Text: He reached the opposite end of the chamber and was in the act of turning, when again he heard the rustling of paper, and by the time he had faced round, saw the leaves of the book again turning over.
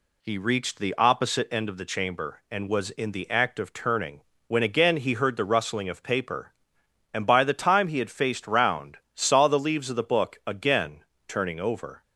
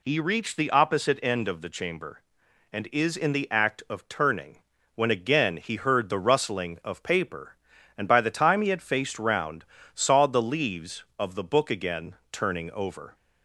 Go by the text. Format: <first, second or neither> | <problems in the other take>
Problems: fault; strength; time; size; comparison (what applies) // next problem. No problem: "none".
first | says "is" for "was"; at 2.9 s // pauses between "again" and "turning"; slight; at 12.1 s; 0.16 s long; slight in the first